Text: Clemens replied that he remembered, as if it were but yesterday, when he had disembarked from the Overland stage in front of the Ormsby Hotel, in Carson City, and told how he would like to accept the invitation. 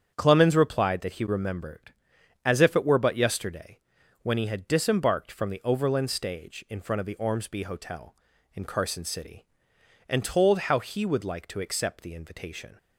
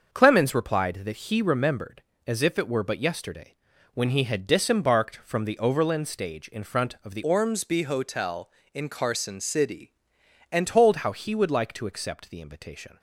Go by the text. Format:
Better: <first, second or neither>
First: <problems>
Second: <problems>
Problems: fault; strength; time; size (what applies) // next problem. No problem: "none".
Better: first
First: starts louder than the rest; strong; until 1.1 s; 8 dB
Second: starts louder than the rest; until 1.1 s; 6.5 dB // changes voice from "Ormsby" to "and"; from 7.2 to 10.6 s; 3.4 s long